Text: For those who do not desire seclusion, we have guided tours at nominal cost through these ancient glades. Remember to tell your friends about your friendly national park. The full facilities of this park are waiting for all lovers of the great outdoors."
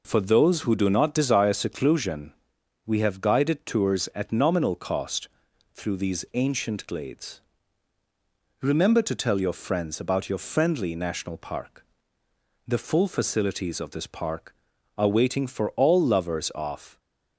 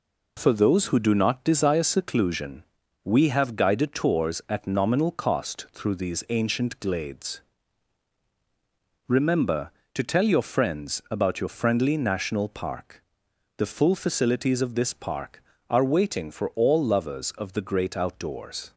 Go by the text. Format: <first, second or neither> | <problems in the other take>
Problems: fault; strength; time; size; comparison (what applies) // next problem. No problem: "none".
second | pauses between "cost" and "through"; noticeable; at 5.2 s; 0.46 s long // stops before "the great outdoors"; at 16.9 s